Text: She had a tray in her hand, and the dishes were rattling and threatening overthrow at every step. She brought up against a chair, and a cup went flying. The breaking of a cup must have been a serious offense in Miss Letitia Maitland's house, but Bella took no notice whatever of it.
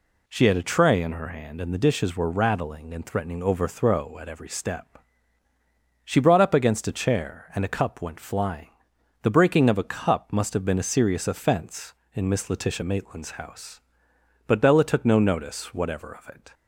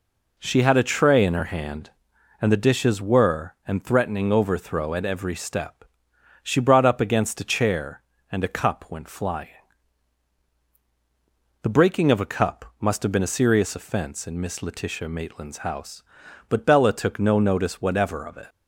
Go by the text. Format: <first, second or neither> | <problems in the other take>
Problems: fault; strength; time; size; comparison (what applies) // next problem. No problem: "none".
first | skips "rattling"; at 3.6 s